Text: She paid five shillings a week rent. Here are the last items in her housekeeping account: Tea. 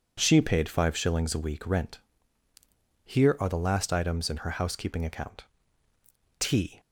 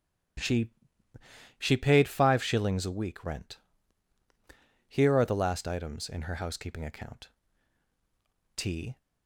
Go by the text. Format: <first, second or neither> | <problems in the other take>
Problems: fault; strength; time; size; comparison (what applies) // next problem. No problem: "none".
first | starts louder than the rest; strong; until 2.2 s; 12.5 dB // says "She" twice; at 1.5 s